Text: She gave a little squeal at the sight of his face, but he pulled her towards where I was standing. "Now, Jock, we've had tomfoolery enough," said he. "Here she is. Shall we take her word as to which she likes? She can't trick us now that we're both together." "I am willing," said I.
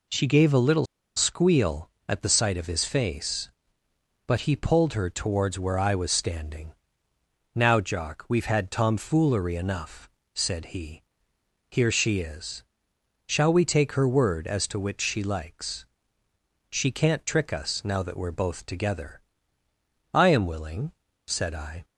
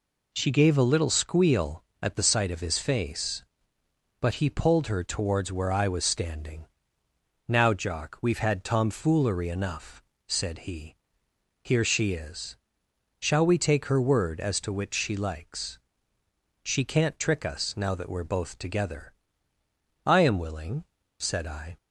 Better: second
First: pauses between "little" and "squeal"; slight; at 0.8 s; 0.30 s long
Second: none

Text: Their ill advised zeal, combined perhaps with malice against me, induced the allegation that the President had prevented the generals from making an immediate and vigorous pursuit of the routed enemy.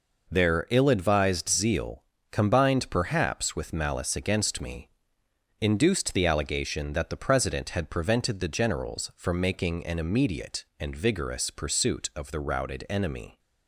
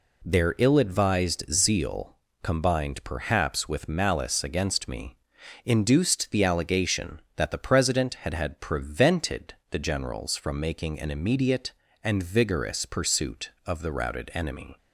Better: first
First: none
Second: says "had" twice; at 8.3 s // pauses between "prevented" and "the"; slight; at 9.5 s; 0.16 s long

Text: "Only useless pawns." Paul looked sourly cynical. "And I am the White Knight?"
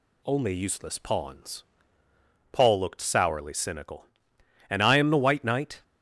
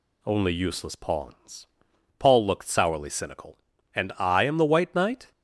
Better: neither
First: none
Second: none

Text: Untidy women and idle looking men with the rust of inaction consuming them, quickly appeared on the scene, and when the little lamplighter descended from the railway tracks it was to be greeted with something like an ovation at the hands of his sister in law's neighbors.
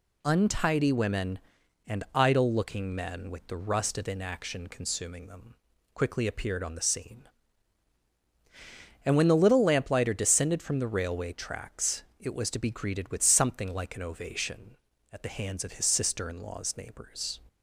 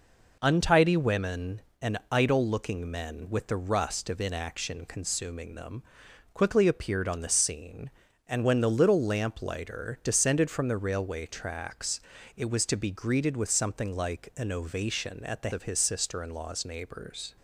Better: first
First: pauses between "tracks" and "it"; slight; at 12.0 s; 0.16 s long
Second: pauses between "tracks" and "it"; slight; at 12.0 s; 0.36 s long // skips "hands"; at 15.5 s

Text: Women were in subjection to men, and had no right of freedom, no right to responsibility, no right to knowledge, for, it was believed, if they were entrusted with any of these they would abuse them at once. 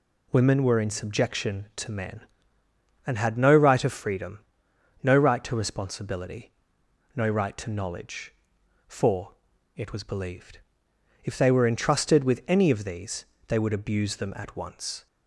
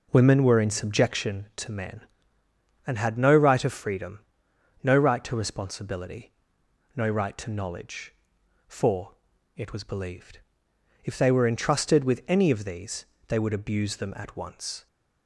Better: first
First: pauses between "these" and "they"; slight; at 13.2 s; 0.22 s long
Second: starts louder than the rest; noticeable; until 1.3 s; 5 dB // pauses between "these" and "they"; slight; at 13.0 s; 0.22 s long

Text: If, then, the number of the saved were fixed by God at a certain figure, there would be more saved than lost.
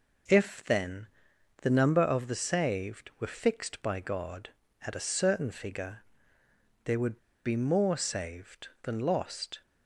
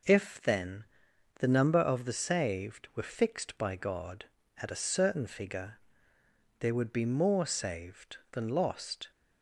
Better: second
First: pauses between "would" and "be"; slight; at 7.1 s; 0.27 s long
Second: none

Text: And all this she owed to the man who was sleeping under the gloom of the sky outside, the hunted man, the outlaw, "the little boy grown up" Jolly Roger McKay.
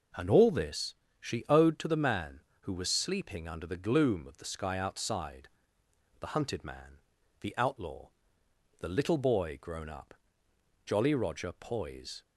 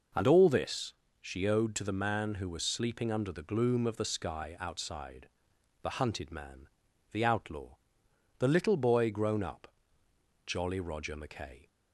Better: second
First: pauses between "this" and "she"; slight; at 0.9 s; 0.26 s long // pauses between "up" and "Jolly"; noticeable; at 10.1 s; 0.70 s long // says "Poise" for "McKay"; at 11.5 s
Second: pauses between "this" and "she"; slight; at 0.9 s; 0.28 s long // pauses between "up" and "Jolly"; noticeable; at 9.6 s; 0.78 s long

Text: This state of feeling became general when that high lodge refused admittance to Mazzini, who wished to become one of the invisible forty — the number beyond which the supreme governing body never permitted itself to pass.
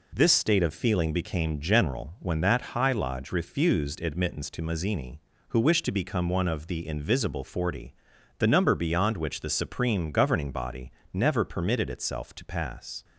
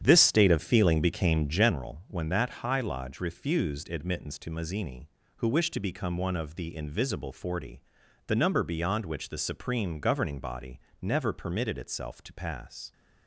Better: first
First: pauses between "body" and "never"; slight; at 10.9 s; 0.20 s long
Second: starts louder than the rest; strong; until 1.7 s; 9 dB // pauses between "body" and "never"; slight; at 10.8 s; 0.20 s long

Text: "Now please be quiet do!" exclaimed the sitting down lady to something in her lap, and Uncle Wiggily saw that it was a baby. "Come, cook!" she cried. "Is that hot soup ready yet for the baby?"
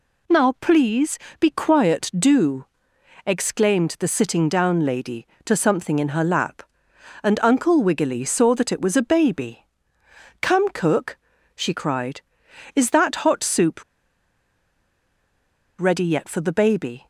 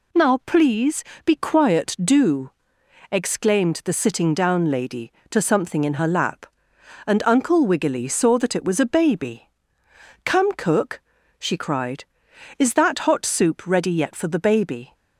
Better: second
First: pauses between "please" and "be"; slight; at 1.1 s; 0.20 s long // pauses between "soup" and "ready"; strong; at 13.8 s; 1.9 s long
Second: pauses between "please" and "be"; slight; at 1.0 s; 0.20 s long

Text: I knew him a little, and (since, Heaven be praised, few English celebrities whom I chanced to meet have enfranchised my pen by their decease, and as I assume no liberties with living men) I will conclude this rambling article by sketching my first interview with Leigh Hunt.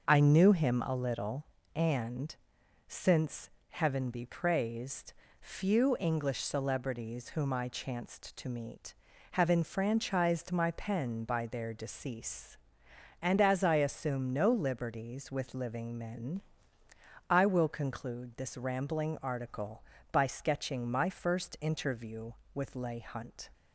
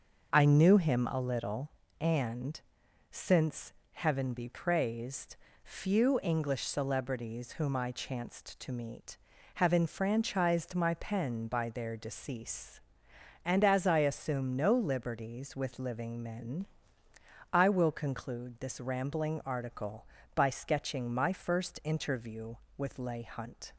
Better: neither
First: starts louder than the rest; until 1.1 s; 6.5 dB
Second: starts louder than the rest; until 1.3 s; 6.5 dB

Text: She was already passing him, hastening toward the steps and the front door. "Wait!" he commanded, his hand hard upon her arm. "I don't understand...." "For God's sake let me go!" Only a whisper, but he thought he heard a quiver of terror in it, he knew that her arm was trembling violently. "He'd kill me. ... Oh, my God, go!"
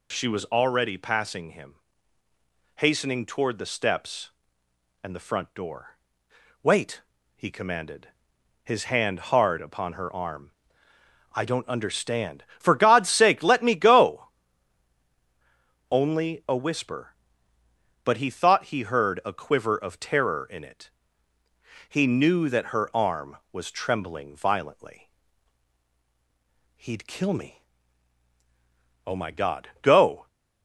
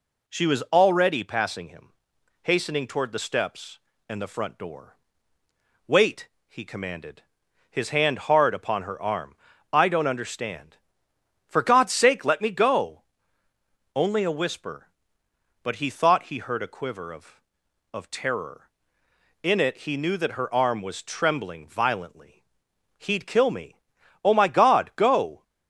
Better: first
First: none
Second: says "of" twice; at 17.9 s

